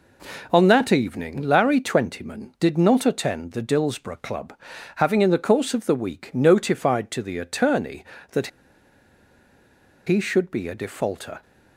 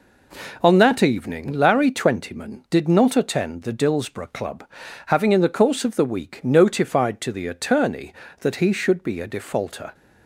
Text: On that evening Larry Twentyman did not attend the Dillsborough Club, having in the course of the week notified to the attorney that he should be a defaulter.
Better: second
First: pauses between "that" and "he"; strong; at 8.4 s; 1.5 s long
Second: none

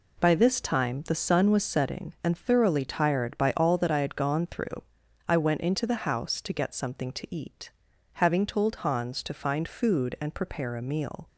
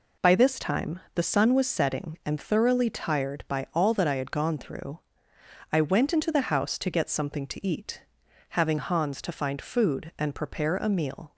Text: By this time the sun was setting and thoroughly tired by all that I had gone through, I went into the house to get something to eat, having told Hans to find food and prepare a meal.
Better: first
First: none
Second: pauses between "time" and "the"; slight; at 0.9 s; 0.16 s long // skips "told"; at 8.7 s

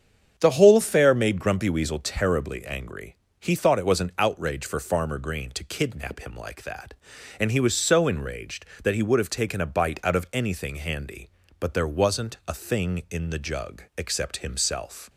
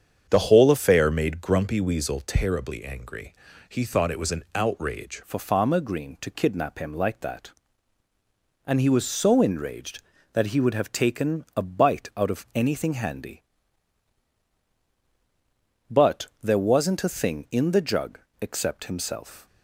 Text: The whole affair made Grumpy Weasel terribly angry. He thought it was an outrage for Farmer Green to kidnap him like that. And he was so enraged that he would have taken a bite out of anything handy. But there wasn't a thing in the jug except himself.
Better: first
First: starts louder than the rest; strong; until 1.3 s; 7.5 dB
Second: starts louder than the rest; strong; until 1.3 s; 7.5 dB // changes voice at "for"; from 5.2 s on; 14.2 s long // pauses between "But" and "there"; slight; at 16.2 s; 0.16 s long // pauses between "jug" and "except"; slight; at 18.1 s; 0.22 s long

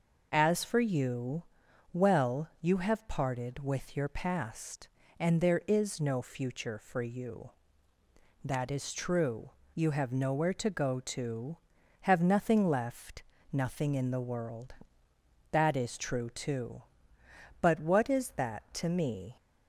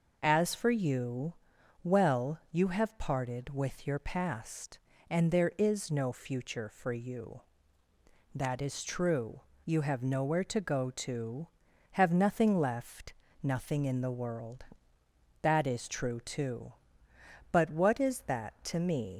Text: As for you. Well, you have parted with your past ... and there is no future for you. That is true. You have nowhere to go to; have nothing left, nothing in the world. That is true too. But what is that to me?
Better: first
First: none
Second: leaves "me" unfinished; at 19.1 s; 70 ms

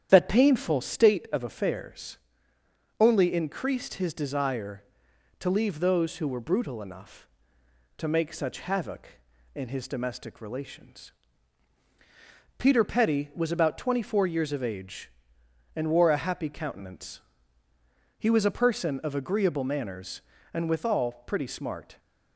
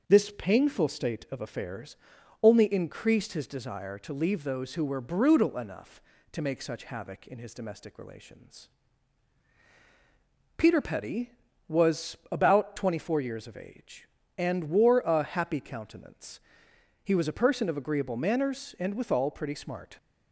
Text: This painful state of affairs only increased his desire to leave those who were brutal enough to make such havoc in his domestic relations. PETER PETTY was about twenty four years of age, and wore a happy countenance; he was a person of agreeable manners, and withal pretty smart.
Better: second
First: starts louder than the rest; strong; until 1.1 s; 9.5 dB // says "That" for "This"; at 0.1 s // pauses between "affairs" and "only"; noticeable; at 2.1 s; 0.82 s long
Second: starts louder than the rest; noticeable; until 1.1 s; 6 dB // pauses between "affairs" and "only"; noticeable; at 1.9 s; 0.46 s long

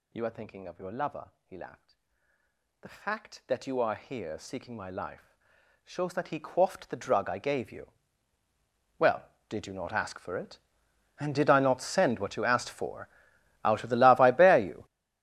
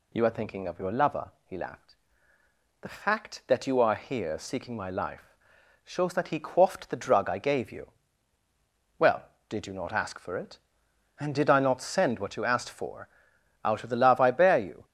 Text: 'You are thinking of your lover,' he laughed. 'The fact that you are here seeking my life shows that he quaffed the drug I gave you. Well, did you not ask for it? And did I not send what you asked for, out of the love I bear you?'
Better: second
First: gets louder; strong; throughout; 17 dB // pauses between "life" and "shows"; noticeable; at 5.3 s; 0.50 s long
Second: pauses between "life" and "shows"; noticeable; at 5.3 s; 0.50 s long

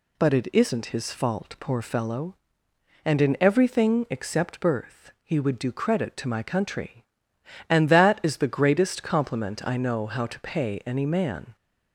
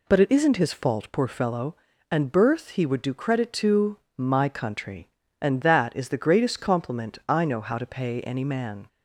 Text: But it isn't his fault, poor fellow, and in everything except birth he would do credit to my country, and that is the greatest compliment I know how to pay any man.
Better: first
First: none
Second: skips "in everything except"; at 2.3 s // pauses between "to" and "my"; slight; at 3.9 s; 0.20 s long

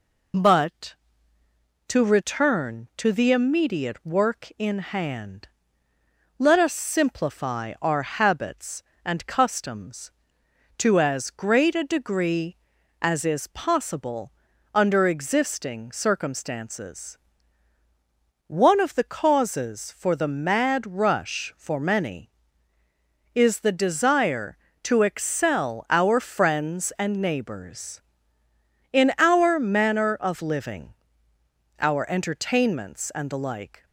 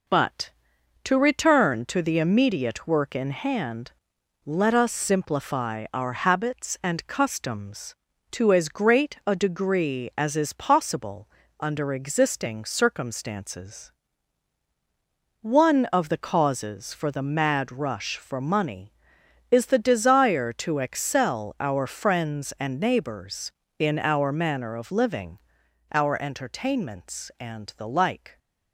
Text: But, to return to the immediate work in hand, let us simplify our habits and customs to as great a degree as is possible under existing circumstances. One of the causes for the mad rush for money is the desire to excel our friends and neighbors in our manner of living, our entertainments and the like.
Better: second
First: pauses between "possible" and "under"; at 14.3 s; 0.42 s long // says "many" for "money"; at 21.7 s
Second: pauses between "possible" and "under"; slight; at 11.2 s; 0.32 s long

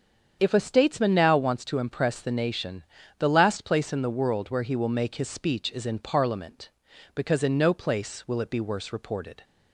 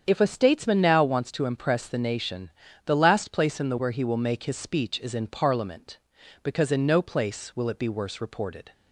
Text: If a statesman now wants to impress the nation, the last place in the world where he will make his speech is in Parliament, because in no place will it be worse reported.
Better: first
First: starts louder than the rest; strong; until 1.4 s; 8 dB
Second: starts louder than the rest; strong; until 1.0 s; 8 dB // skips "world"; at 3.7 s

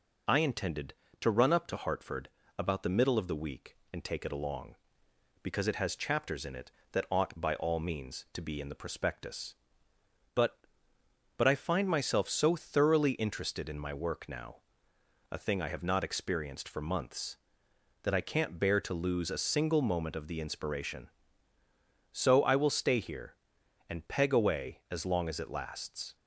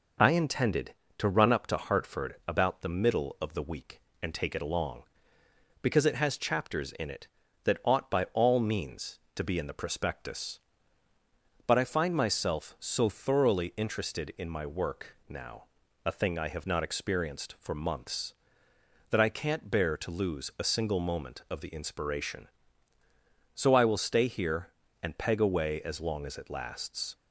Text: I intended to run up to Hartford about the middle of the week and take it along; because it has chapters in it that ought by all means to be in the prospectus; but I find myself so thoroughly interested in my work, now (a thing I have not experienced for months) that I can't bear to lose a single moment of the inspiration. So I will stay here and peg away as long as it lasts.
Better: second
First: pauses between "Hartford" and "about"; slight; at 2.2 s; 0.28 s long // says "but" twice; at 11.3 s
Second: none

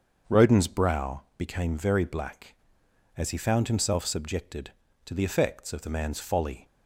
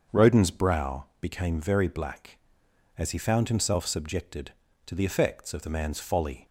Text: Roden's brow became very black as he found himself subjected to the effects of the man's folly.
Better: neither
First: starts louder than the rest; until 1.4 s; 6.5 dB // pauses between "brow" and "became"; slight; at 1.2 s; 0.16 s long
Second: starts louder than the rest; until 1.2 s; 6.5 dB // pauses between "brow" and "became"; slight; at 1.0 s; 0.16 s long

